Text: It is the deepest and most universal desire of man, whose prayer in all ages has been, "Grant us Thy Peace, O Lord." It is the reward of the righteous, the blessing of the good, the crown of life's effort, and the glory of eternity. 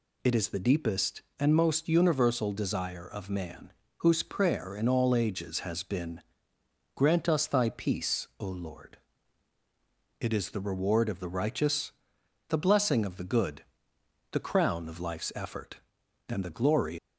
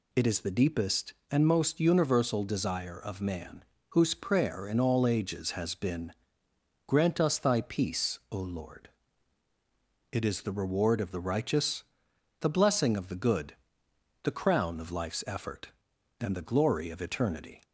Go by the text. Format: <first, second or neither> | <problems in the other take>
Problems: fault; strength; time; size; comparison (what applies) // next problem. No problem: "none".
second | stops before "of eternity"; at 16.9 s